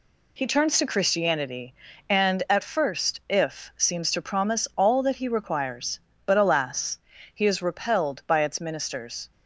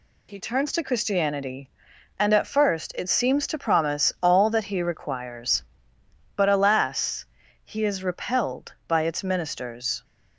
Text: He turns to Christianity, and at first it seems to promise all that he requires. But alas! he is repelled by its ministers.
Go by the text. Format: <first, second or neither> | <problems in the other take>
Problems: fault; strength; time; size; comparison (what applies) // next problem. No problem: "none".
second | says "if" for "it"; at 3.2 s